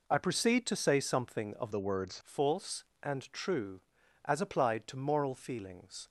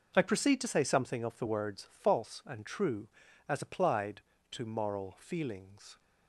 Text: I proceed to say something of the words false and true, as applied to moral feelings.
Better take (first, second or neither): second